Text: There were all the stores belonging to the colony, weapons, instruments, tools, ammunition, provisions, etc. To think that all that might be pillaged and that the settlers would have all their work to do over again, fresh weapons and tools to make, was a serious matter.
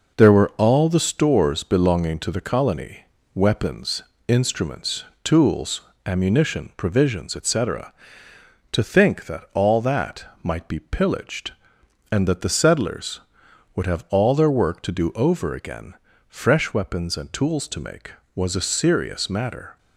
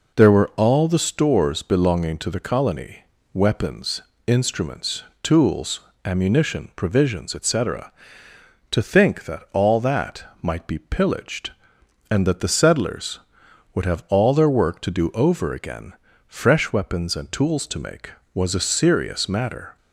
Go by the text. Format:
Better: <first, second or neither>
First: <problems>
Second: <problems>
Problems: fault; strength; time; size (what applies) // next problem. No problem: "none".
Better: second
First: gets quieter; noticeable; throughout; 5 dB // pauses between "that" and "might"; slight; at 10.2 s; 0.20 s long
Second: pauses between "that" and "might"; slight; at 10.2 s; 0.20 s long